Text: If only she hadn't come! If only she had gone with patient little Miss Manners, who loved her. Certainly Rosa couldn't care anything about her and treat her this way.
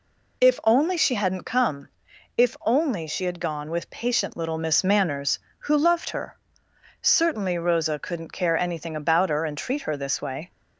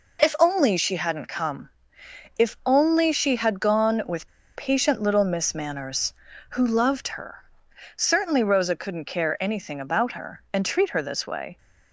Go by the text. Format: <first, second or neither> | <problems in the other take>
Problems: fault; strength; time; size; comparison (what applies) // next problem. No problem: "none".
first | pauses between "with" and "patient"; slight; at 4.2 s; 0.26 s long